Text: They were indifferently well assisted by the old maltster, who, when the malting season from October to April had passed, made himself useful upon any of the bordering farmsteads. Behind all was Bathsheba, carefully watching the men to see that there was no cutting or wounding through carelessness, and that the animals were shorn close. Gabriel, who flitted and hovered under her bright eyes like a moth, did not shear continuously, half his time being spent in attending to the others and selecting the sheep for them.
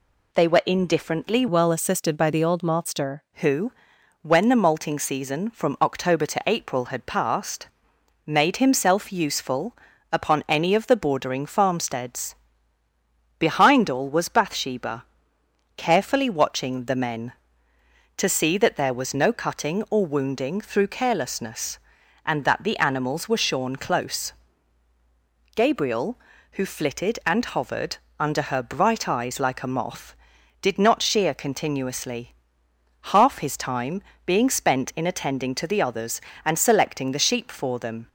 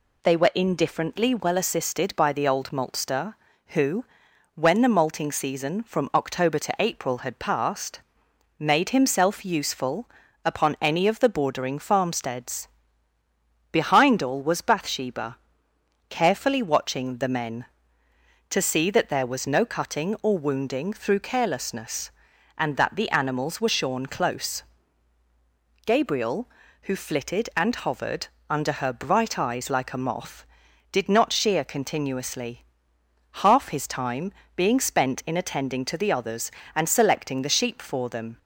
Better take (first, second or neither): second